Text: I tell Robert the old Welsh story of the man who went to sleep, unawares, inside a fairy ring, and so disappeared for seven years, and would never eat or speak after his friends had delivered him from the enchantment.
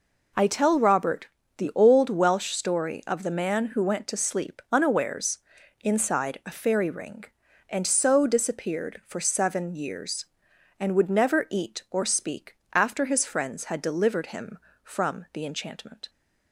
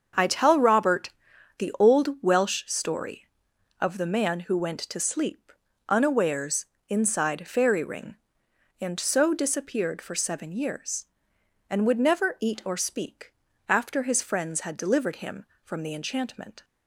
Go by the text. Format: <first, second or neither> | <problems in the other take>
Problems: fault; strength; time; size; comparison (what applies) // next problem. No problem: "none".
first | starts louder than the rest; until 1.6 s; 7 dB // pauses between "Robert" and "the"; noticeable; at 1.1 s; 0.48 s long; slight in the first // skips "a"; at 7.4 s // pauses between "speak" and "after"; slight; at 13.3 s; 0.36 s long; slight in the first